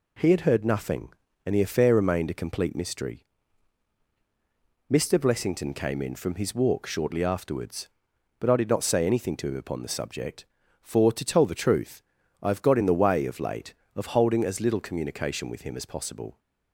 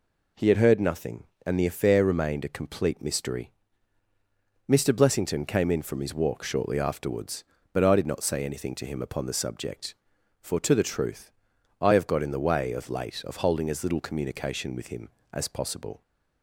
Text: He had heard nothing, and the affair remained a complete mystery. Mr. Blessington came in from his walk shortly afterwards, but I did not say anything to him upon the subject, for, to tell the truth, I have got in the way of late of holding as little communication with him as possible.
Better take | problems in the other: first | skips "tell"; at 10.7 s

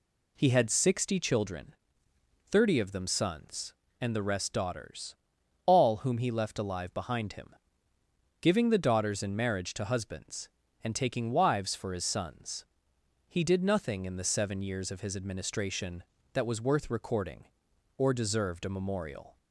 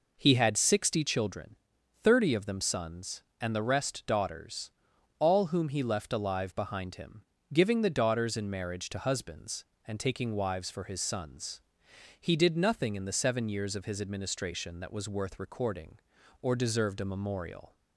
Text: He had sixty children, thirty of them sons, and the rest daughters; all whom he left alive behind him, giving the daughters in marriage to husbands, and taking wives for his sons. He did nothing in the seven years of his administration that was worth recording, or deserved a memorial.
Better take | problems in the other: neither | none

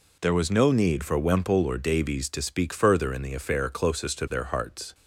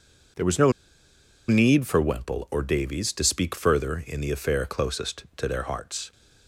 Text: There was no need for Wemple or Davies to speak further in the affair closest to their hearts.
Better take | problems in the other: first | pauses between "no" and "need"; noticeable; at 0.7 s; 0.76 s long

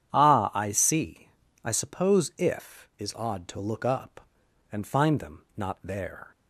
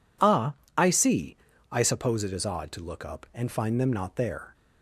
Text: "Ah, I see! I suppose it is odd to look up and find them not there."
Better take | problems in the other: second | says "if" for "it"; at 2.3 s

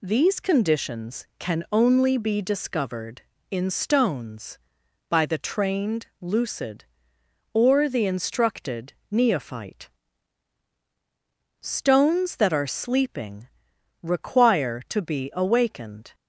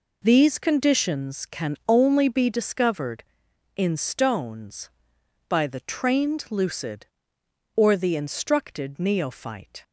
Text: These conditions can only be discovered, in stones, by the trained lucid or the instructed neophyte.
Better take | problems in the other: second | pauses between "trained" and "lucid"; slight; at 6.0 s; 0.16 s long // pauses between "instructed" and "neophyte"; slight; at 8.9 s; 0.16 s long // goes on to say "Stones that are sleeping require to be awakened"; strong; from 11.6 s on; 4.5 s long

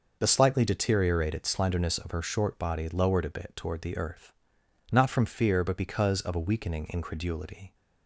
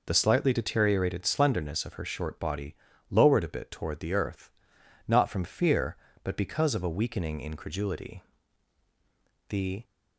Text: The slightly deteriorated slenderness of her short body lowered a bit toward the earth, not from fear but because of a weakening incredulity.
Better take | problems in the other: first | pauses between "body" and "lowered"; slight; at 2.7 s; 0.36 s long // goes on to say "The"; slight; from 9.4 s on; 0.34 s long

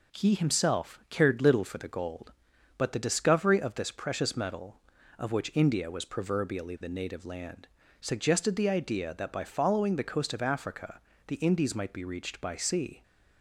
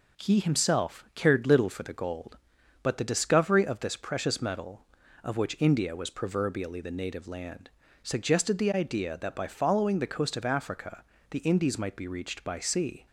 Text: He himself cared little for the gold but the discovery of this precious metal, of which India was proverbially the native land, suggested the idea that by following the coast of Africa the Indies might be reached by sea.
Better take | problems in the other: neither | pauses between "Africa" and "the"; slight; the same in both

